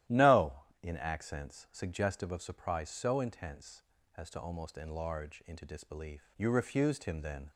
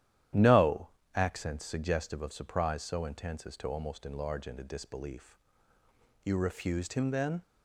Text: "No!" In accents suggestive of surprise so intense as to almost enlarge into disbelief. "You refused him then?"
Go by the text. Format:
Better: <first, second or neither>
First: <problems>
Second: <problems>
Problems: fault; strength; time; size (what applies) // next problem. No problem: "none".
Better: first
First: starts louder than the rest; strong; until 1.2 s; 13 dB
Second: starts louder than the rest; strong; until 1.6 s; 11.5 dB // skips "In"; at 1.0 s